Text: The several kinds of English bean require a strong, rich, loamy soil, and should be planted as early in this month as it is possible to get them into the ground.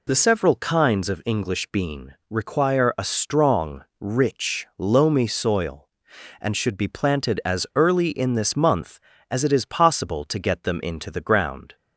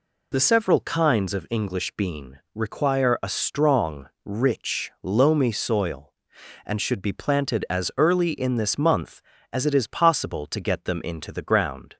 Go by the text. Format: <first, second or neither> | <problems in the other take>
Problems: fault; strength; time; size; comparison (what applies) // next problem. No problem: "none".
neither | pauses between "bean" and "require"; slight; the same in both